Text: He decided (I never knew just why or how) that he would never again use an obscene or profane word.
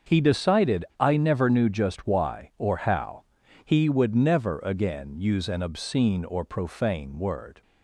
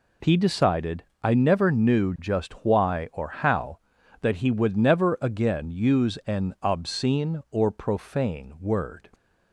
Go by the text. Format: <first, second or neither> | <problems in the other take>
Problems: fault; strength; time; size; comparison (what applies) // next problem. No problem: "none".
second | starts louder than the rest; until 1.2 s; 6.5 dB // skips "that"; at 3.4 s